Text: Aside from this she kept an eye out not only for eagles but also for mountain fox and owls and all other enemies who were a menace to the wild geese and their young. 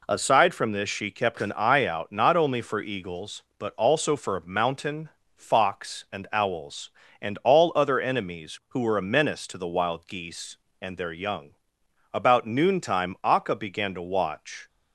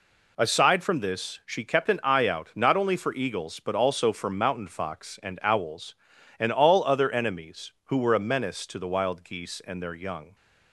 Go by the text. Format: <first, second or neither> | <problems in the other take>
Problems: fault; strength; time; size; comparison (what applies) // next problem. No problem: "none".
second | pauses between "mountain" and "fox"; slight; at 5.0 s; 0.28 s long // goes on to say "About noontime Akka began to watch"; strong; from 12.1 s on; 2.5 s long